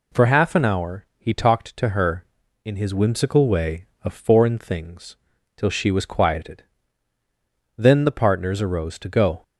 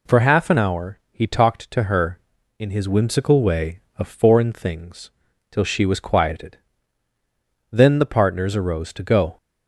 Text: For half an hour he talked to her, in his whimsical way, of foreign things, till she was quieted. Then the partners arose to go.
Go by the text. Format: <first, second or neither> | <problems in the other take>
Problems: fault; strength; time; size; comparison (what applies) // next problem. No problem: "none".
neither | none